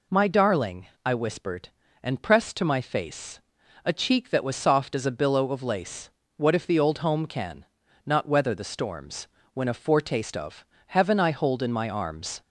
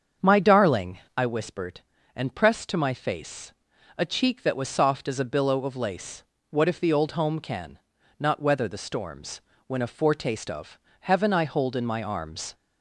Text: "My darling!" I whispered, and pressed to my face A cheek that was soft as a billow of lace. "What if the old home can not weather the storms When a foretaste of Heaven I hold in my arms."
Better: first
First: pauses between "face" and "A"; at 3.3 s; 0.44 s long // pauses between "can" and "not"; at 7.6 s; 0.40 s long // pauses between "storms" and "When"; slight; at 9.2 s; 0.26 s long // pauses between "of" and "Heaven"; slight; at 10.6 s; 0.24 s long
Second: starts louder than the rest; until 1.3 s; 7 dB // pauses between "face" and "A"; at 3.5 s; 0.44 s long // pauses between "can" and "not"; at 7.7 s; 0.40 s long // pauses between "storms" and "When"; slight; at 9.4 s; 0.26 s long // pauses between "of" and "Heaven"; slight; at 10.7 s; 0.24 s long

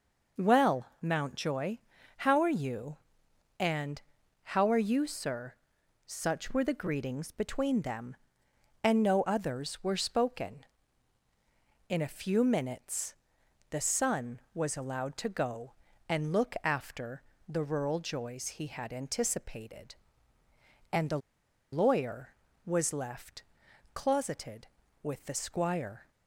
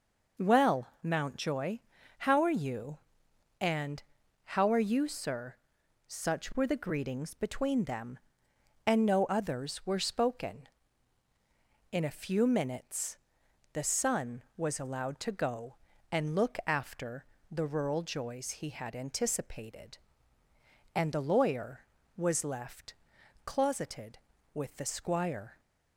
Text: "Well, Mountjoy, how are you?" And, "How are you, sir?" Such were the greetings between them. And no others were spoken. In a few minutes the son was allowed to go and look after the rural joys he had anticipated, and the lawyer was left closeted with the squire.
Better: second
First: pauses between "minutes" and "the"; noticeable; at 13.1 s; 0.56 s long // pauses between "after" and "the"; slight; at 17.2 s; 0.26 s long // pauses between "the" and "lawyer"; noticeable; at 21.1 s; 0.53 s long // pauses between "left" and "closeted"; noticeable; at 23.4 s; 0.50 s long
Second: pauses between "minutes" and "the"; noticeable; at 13.1 s; 0.56 s long // pauses between "after" and "the"; slight; at 17.2 s; 0.26 s long // pauses between "left" and "closeted"; noticeable; at 22.9 s; 0.50 s long

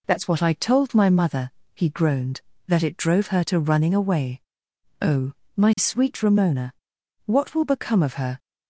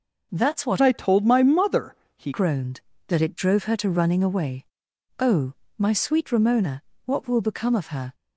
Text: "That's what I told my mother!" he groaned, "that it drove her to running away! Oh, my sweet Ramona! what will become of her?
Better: first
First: none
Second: changes voice from "I" to "he"; from 0.8 to 2.3 s; 1.5 s long

